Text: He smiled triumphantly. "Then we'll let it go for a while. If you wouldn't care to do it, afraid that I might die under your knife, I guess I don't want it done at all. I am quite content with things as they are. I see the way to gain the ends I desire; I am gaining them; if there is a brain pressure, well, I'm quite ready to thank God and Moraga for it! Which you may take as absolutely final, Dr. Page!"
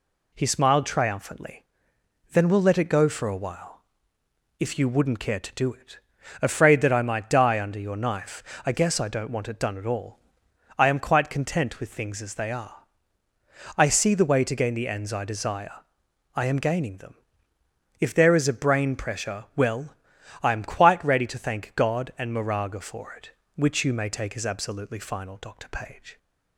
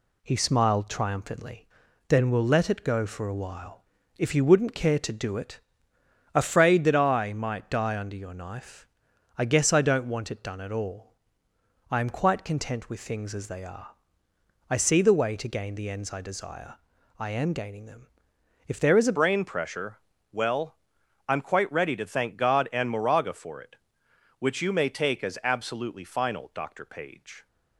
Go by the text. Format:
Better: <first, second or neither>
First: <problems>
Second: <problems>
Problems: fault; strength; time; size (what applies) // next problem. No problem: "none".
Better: first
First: none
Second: changes voice at "brain"; from 19.1 s on; 8.3 s long